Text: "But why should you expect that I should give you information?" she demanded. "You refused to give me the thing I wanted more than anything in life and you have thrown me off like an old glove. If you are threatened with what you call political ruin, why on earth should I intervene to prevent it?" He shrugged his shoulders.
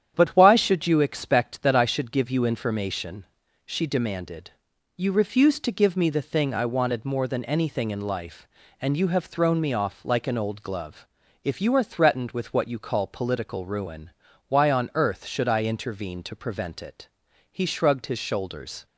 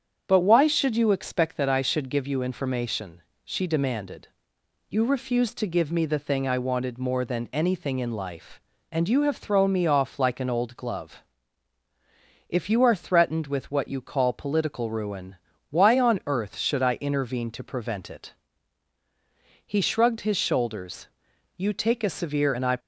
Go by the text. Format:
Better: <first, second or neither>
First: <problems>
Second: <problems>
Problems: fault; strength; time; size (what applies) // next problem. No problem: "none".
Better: first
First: starts louder than the rest; strong; until 1.1 s; 9.5 dB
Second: starts louder than the rest; strong; until 1.2 s; 8 dB // goes on to say "You take a severe and I"; noticeable; from 21.5 s on; 1.2 s long